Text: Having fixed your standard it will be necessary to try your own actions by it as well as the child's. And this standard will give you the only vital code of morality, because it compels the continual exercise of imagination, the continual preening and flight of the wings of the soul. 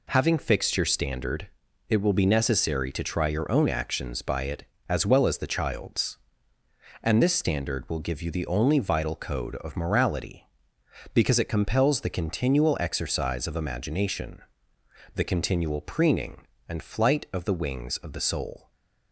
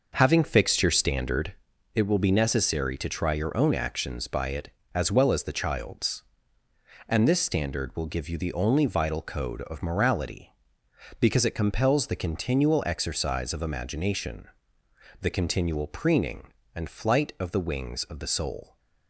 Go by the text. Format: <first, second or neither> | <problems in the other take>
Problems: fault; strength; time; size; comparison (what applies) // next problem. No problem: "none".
first | starts louder than the rest; noticeable; until 1.8 s; 6 dB // pauses between "standard" and "it"; at 1.5 s; 0.42 s long; also in the first